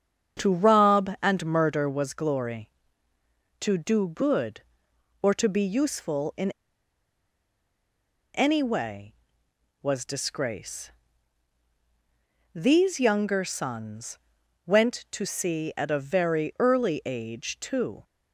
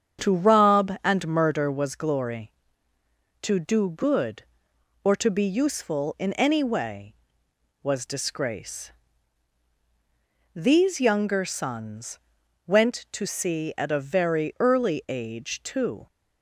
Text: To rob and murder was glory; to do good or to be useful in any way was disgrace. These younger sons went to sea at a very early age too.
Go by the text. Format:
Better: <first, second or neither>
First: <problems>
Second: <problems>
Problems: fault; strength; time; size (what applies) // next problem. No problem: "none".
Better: second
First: starts louder than the rest; strong; until 1.4 s; 8 dB // pauses between "in" and "any"; strong; at 6.5 s; 1.8 s long // pauses between "sons" and "went"; noticeable; at 14.1 s; 0.48 s long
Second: starts louder than the rest; strong; until 1.3 s; 8 dB // pauses between "sons" and "went"; noticeable; at 12.1 s; 0.48 s long